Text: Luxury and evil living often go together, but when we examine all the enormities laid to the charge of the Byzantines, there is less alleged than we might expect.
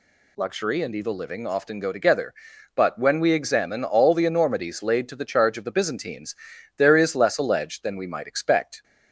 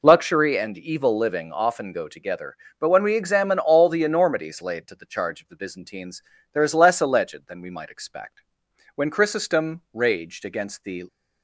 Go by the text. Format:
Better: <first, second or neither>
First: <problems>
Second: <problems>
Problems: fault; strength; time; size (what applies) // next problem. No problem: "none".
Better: first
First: none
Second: goes on to say "When Chrysostom raged against the"; strong; from 8.9 s on; 2.1 s long